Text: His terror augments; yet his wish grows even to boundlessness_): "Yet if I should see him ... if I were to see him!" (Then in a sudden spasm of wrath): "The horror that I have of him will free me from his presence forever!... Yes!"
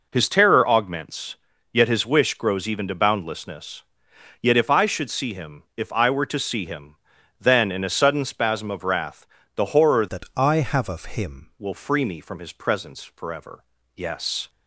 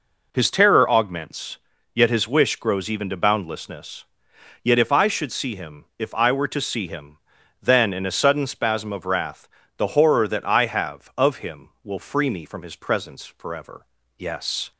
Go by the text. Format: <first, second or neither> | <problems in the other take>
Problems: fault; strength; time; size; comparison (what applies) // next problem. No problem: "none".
second | changes voice from "that" to "him"; from 10.0 to 11.5 s; 1.5 s long